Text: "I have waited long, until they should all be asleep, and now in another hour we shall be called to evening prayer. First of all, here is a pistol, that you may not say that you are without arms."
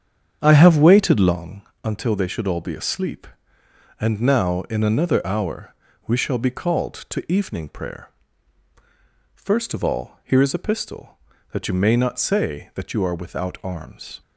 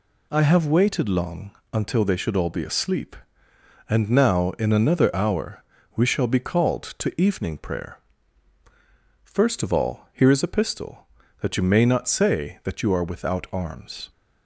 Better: second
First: starts louder than the rest; strong; until 1.4 s; 8.5 dB // pauses between "hour" and "we"; slight; at 5.7 s; 0.32 s long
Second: pauses between "hour" and "we"; slight; at 5.6 s; 0.32 s long

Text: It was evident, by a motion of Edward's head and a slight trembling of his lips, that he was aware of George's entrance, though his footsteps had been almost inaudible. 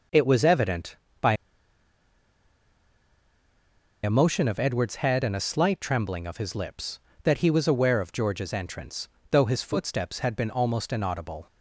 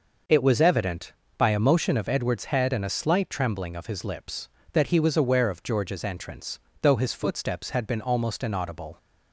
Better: second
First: pauses between "by" and "a"; strong; at 1.3 s; 2.7 s long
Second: none

